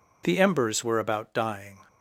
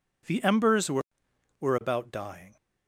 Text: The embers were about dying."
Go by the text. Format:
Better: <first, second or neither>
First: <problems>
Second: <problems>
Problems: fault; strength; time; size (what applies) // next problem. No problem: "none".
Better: first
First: none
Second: says "were" twice; at 1.5 s